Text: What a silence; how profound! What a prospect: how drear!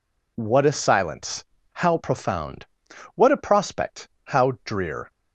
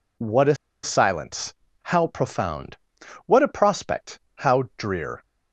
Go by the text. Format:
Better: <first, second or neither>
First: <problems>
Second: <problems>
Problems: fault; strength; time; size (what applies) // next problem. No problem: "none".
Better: first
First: none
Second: pauses between "a" and "silence"; slight; at 0.5 s; 0.27 s long